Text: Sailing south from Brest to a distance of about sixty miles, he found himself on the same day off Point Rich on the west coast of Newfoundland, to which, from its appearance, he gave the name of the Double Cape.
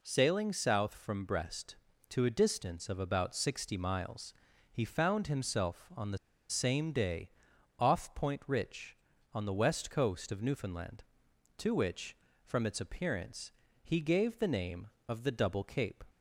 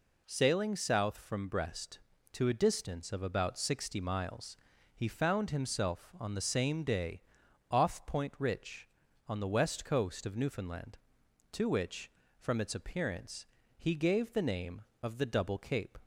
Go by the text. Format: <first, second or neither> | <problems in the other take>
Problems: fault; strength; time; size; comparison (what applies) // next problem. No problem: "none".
second | pauses between "the" and "same"; slight; at 6.1 s; 0.32 s long // pauses between "day" and "off"; noticeable; at 7.2 s; 0.50 s long; noticeable in the second